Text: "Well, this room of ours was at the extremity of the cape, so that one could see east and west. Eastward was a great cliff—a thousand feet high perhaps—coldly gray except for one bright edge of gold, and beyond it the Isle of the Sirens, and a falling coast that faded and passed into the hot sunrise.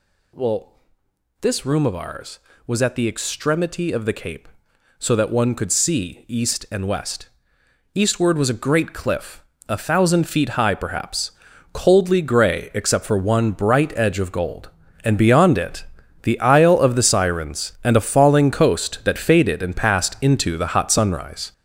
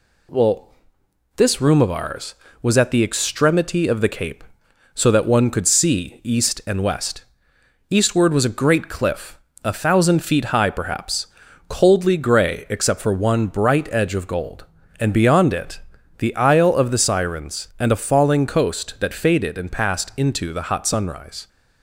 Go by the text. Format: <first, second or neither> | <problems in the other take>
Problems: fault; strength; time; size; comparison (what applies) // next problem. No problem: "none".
second | gets louder; strong; throughout; 7.5 dB // pauses between "it" and "the"; at 15.8 s; 0.38 s long; also in the second